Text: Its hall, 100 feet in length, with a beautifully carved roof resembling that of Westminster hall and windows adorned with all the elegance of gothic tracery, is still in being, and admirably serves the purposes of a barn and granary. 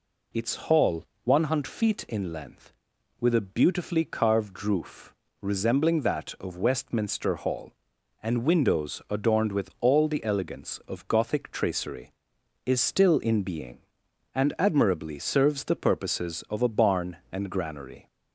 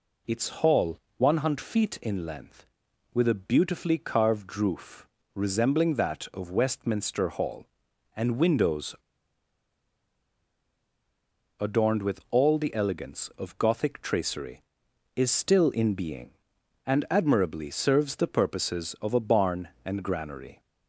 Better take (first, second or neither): first